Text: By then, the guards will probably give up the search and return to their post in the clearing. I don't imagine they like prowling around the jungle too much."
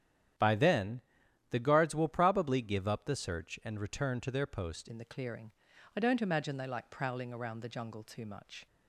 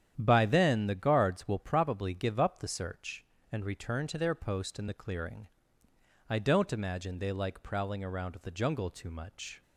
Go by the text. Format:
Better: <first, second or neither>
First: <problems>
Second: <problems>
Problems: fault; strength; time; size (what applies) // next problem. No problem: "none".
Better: second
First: starts louder than the rest; strong; until 1.8 s; 10 dB // changes voice at "in"; from 4.9 s on; 3.7 s long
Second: starts louder than the rest; strong; until 1.1 s; 9.5 dB